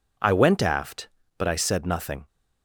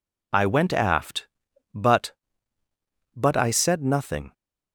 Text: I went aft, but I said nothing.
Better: first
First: none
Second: says "but" twice; at 3.1 s

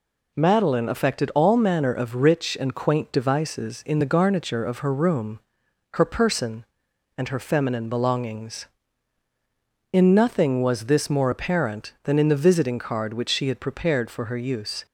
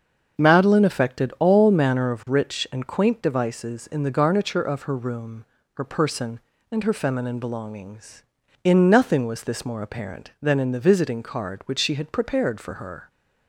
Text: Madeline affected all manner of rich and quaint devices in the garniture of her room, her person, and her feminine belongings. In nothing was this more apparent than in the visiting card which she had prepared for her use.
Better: first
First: none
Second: starts louder than the rest; until 1.4 s; 6.5 dB // stops before "use"; at 13.0 s

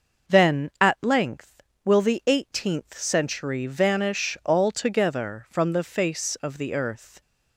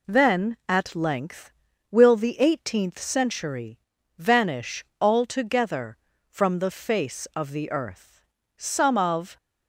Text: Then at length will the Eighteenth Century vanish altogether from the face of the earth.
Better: first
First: none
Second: pauses between "Century" and "vanish"; at 3.7 s; 0.40 s long // pauses between "vanish" and "altogether"; slight; at 4.8 s; 0.16 s long // goes on to say "Some of"; noticeable; from 8.5 s on; 0.80 s long

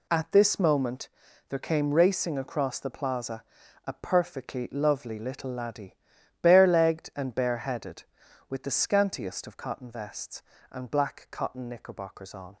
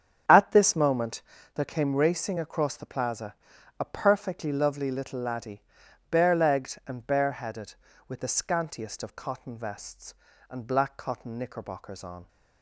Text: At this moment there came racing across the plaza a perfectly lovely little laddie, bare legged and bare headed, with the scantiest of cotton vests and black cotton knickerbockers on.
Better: first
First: pauses between "moment" and "there"; at 1.0 s; 0.40 s long // pauses between "plaza" and "a"; noticeable; at 3.4 s; 0.46 s long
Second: starts louder than the rest; strong; until 1.5 s; 8 dB // pauses between "moment" and "there"; slight; at 1.2 s; 0.34 s long // pauses between "plaza" and "a"; at 3.3 s; 0.42 s long

